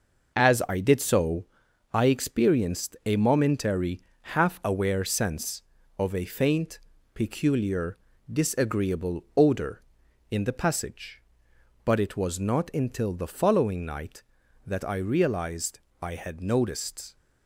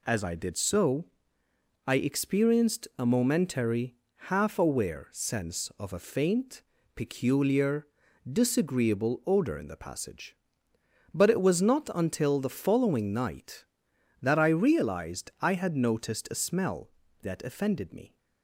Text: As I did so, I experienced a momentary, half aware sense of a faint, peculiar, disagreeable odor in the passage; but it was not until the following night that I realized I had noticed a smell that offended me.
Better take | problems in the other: second | pauses between "realized" and "I"; slight; at 15.7 s; 0.22 s long // stops before "a smell that offended me"; at 17.1 s

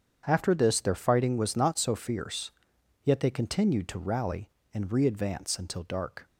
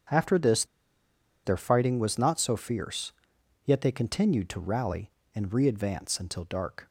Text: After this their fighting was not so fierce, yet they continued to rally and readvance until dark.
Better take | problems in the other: first | starts louder than the rest; strong; until 1.9 s; 7.5 dB; strong in the first // pauses between "this" and "their"; noticeable; at 0.6 s; 0.81 s long

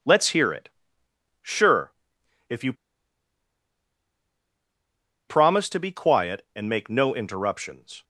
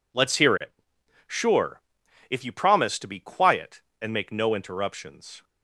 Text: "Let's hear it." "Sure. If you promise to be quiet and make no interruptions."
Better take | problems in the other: second | pauses between "you" and "promise"; strong; at 2.7 s; 2.5 s long

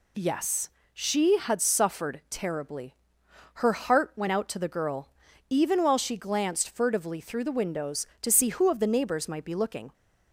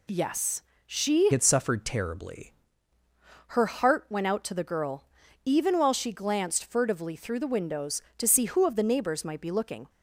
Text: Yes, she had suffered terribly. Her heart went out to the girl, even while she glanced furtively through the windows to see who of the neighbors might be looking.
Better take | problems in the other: first | changes voice from "had" to "terribly"; from 1.3 to 2.5 s; 1.2 s long

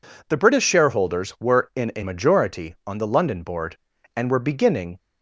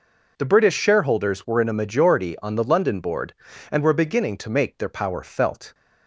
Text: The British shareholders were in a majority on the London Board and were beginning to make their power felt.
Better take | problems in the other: second | stops before "to make their power felt"; at 4.9 s

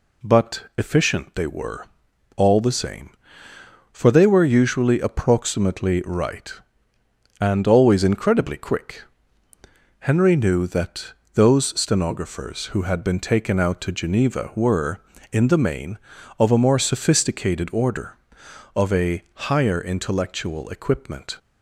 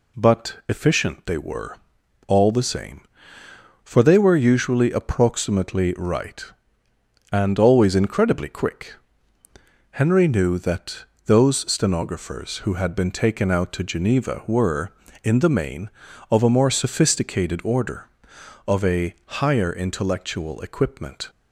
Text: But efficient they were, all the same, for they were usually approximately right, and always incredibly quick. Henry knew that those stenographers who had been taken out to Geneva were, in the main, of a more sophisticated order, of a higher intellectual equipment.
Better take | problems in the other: neither | pauses between "that" and "those"; slight; the same in both

